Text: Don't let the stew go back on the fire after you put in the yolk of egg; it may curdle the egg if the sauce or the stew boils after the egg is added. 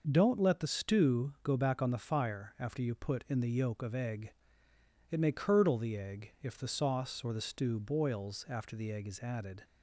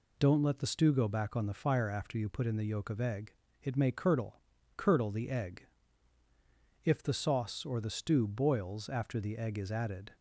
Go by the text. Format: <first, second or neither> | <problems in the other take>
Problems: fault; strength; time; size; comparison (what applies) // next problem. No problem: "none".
first | says "curdle" twice; at 4.7 s // pauses between "egg" and "if"; at 5.6 s; 1.2 s long